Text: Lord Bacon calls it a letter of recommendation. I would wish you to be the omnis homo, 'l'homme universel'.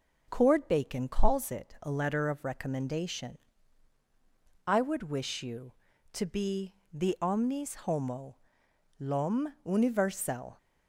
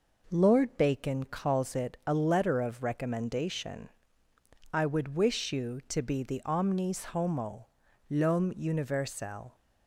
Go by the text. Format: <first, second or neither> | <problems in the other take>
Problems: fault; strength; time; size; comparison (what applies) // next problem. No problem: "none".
second | says "Cord" for "Lord"; at 0.2 s // pauses between "be" and "the"; slight; at 6.7 s; 0.18 s long